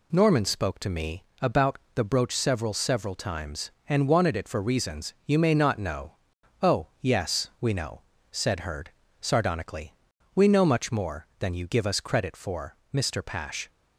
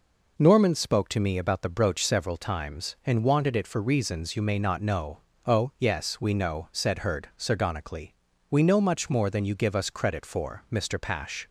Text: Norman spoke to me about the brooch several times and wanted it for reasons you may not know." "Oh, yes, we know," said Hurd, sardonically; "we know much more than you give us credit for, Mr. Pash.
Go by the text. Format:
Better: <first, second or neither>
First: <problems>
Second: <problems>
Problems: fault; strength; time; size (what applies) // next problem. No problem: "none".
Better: second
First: pauses between "me" and "about"; slight; at 1.2 s; 0.18 s long // pauses between "about" and "the"; slight; at 1.7 s; 0.18 s long // says "several" twice; at 2.7 s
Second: none